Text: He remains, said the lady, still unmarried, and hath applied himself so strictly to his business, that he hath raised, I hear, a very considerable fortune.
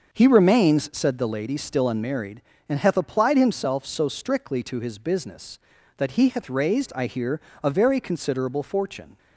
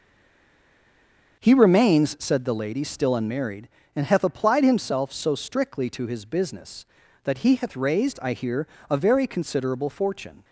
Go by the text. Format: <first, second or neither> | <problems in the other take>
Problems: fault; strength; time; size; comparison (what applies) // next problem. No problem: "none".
first | stays silent before the first word; noticeable; until 1.4 s; 1.4 s long // starts louder than the rest; until 2.4 s; 6.5 dB; also in the first